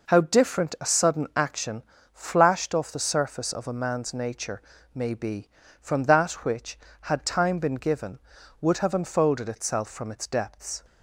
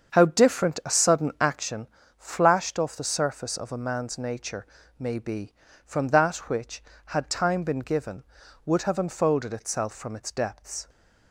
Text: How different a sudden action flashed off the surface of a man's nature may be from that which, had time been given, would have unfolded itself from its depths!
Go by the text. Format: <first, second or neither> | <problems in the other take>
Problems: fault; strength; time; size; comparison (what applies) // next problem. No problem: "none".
first | starts louder than the rest; until 1.7 s; 7 dB // pauses between "action" and "flashed"; slight; at 1.8 s; 0.32 s long; slight in the first // pauses between "nature" and "may"; slight; at 4.6 s; 0.32 s long; slight in the first